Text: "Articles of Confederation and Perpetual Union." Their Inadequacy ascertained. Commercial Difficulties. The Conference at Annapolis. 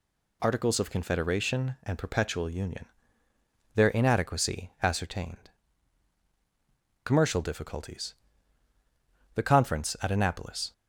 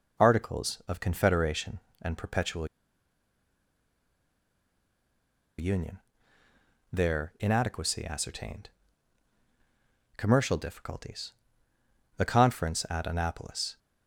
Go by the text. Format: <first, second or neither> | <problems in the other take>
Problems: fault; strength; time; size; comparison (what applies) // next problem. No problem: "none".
first | pauses between "Perpetual" and "Union"; strong; at 2.6 s; 2.9 s long